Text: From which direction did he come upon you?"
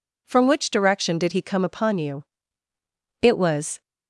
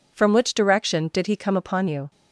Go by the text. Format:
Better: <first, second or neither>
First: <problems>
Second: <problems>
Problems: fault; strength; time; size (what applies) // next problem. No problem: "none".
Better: second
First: goes on to say "It was"; from 3.2 s on; 0.60 s long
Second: none